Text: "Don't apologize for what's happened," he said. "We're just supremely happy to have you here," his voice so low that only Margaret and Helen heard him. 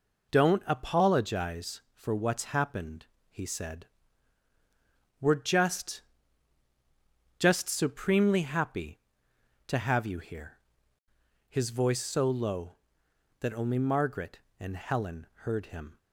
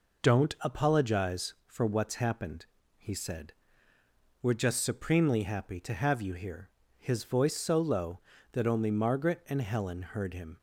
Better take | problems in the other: second | says "just" twice; at 7.3 s // pauses between "Helen" and "heard"; slight; at 15.2 s; 0.18 s long

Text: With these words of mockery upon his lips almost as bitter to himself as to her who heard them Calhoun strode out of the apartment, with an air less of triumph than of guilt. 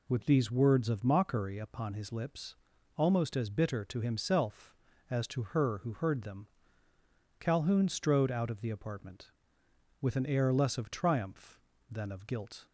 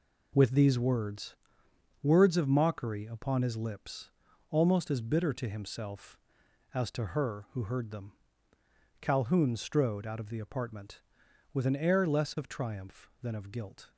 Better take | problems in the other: first | says "words" twice; at 2.0 s // pauses between "lips" and "almost"; at 4.0 s; 0.40 s long; also in the first // pauses between "them" and "Calhoun"; noticeable; at 8.1 s; 0.86 s long; noticeable in the first

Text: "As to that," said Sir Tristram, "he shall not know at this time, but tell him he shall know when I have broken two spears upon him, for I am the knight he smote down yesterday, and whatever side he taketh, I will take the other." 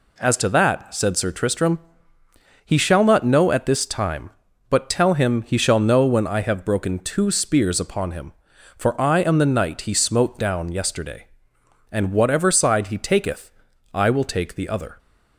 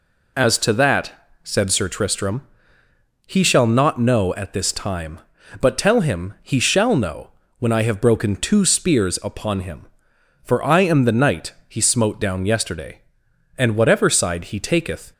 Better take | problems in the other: first | pauses between "know" and "when"; slight; at 7.3 s; 0.28 s long // pauses between "knight" and "he"; slight; at 11.5 s; 0.16 s long // stops before "I will take the other"; at 15.1 s

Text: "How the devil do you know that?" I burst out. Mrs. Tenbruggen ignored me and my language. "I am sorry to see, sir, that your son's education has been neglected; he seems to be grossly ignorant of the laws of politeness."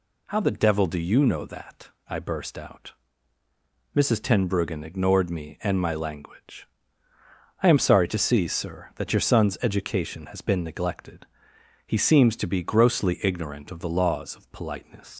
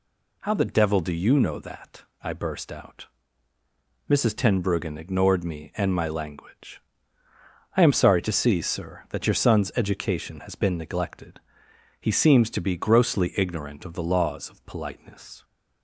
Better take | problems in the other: second | leaves "politeness" unfinished; at 15.1 s; 115 ms

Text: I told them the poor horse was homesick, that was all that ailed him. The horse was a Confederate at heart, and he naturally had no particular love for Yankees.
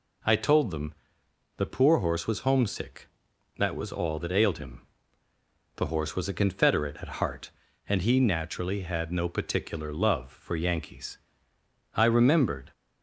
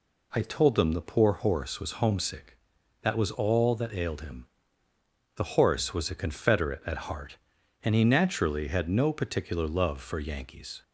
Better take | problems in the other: second | pauses between "them" and "the"; noticeable; at 0.9 s; 0.64 s long // goes on to say "I remembered"; noticeable; from 11.9 s on; 0.78 s long

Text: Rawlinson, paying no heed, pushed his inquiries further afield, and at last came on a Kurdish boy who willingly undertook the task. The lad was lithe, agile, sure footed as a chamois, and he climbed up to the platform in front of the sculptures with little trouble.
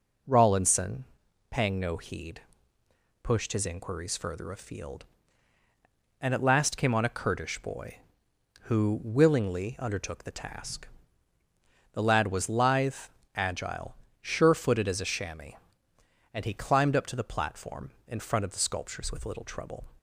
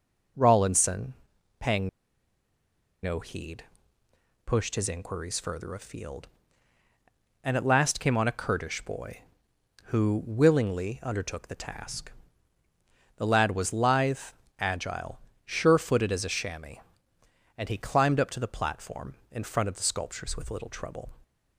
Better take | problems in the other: first | pauses between "paying" and "no"; at 1.8 s; 1.1 s long

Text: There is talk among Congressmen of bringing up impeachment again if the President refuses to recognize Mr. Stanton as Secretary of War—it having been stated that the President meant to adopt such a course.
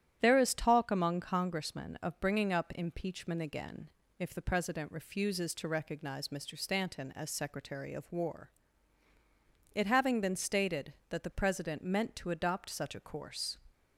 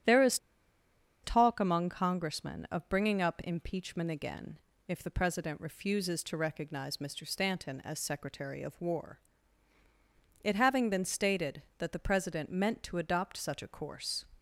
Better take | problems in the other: first | starts louder than the rest; strong; until 1.9 s; 10.5 dB; strong in the first // pauses between "is" and "talk"; noticeable; at 0.3 s; 0.85 s long // pauses between "again" and "if"; slight; at 4.5 s; 0.28 s long; slight in the first

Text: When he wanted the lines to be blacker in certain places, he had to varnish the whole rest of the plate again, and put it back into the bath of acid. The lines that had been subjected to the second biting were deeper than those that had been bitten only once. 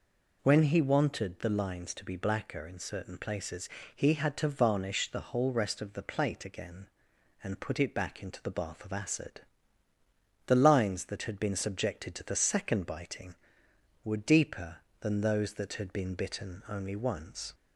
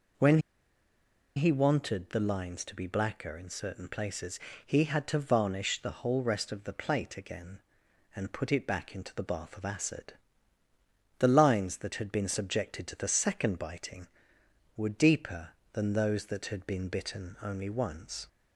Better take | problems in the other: first | pauses between "When" and "he"; noticeable; at 0.3 s; 0.97 s long

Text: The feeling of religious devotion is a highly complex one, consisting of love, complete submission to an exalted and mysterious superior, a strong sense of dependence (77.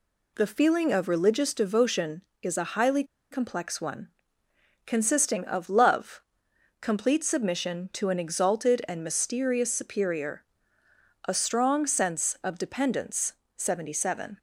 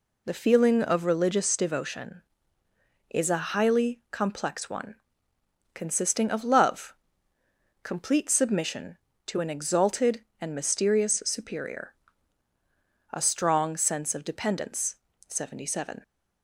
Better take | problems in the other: second | pauses between "highly" and "complex"; slight; at 3.0 s; 0.27 s long

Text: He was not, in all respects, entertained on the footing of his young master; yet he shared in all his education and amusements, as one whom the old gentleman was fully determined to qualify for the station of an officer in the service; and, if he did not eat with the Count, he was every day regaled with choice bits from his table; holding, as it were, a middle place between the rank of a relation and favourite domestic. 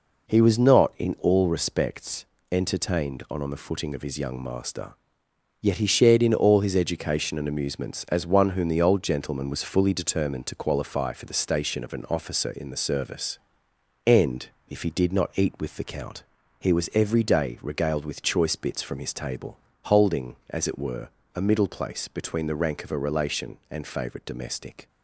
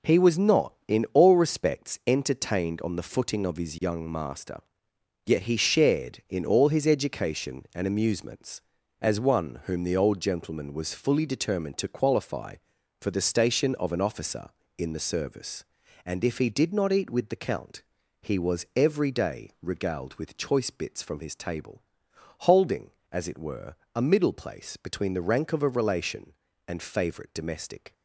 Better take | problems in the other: second | says "on" twice; at 3.4 s

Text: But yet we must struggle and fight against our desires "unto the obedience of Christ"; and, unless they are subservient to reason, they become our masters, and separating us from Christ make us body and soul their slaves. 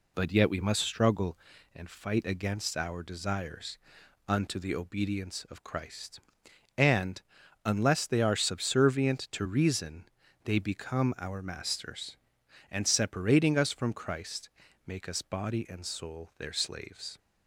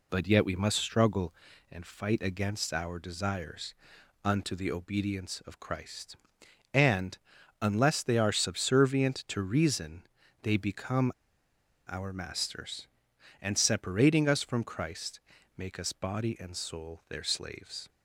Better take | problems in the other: first | pauses between "desires" and "unto"; noticeable; at 3.7 s; 0.50 s long; noticeable in the first // pauses between "become" and "our"; noticeable; at 11.1 s; 0.74 s long // pauses between "Christ" and "make"; slight; at 15.2 s; 0.36 s long; slight in the first

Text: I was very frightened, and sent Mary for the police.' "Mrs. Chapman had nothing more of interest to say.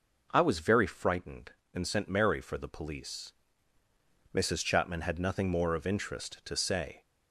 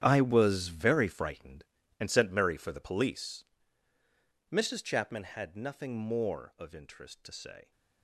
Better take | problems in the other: first | gets quieter; strong; throughout; 15 dB

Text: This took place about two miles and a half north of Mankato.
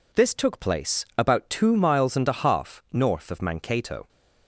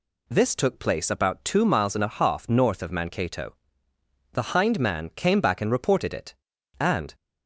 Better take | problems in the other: first | goes on to say "The hind man came back and reported it and"; strong; from 4.3 s on; 2.8 s long

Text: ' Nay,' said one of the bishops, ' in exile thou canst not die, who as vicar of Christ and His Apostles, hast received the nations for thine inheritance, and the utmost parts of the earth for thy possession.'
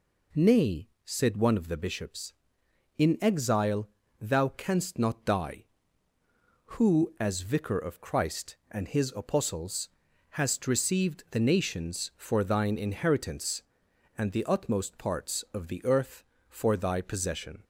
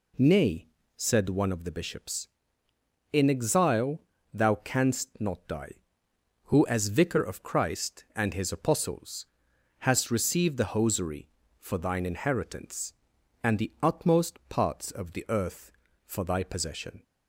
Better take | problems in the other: first | pauses between "exile" and "thou"; slight; at 3.9 s; 0.34 s long; slight in the first // says "hosiery" for "nations"; at 10.7 s

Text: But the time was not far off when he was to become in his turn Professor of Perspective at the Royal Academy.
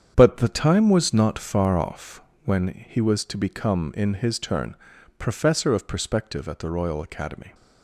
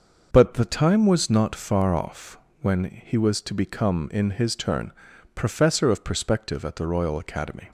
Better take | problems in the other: second | gets quieter; strong; throughout; 9.5 dB // starts louder than the rest; strong; until 1.1 s; 8 dB; noticeable in the second // pauses between "off" and "when"; slight; at 2.2 s; 0.22 s long; slight in the second // pauses between "turn" and "Professor"; at 4.7 s; 0.42 s long; also in the second

